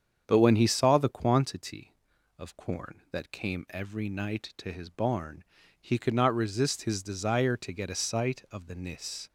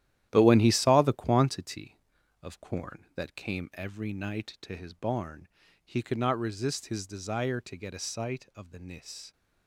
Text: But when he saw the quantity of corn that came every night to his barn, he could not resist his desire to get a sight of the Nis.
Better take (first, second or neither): first